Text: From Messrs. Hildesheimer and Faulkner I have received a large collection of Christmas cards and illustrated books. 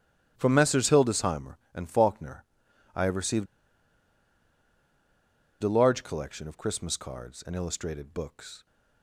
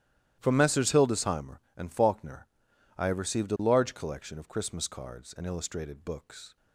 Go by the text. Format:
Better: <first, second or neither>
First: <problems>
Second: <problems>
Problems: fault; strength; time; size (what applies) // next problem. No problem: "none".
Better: second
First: starts louder than the rest; strong; until 1.3 s; 13 dB // pauses between "Faulkner" and "I"; noticeable; at 2.4 s; 0.50 s long // pauses between "received" and "a"; strong; at 3.4 s; 2.1 s long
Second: starts louder than the rest; strong; until 1.4 s; 13 dB // pauses between "Faulkner" and "I"; noticeable; at 2.4 s; 0.50 s long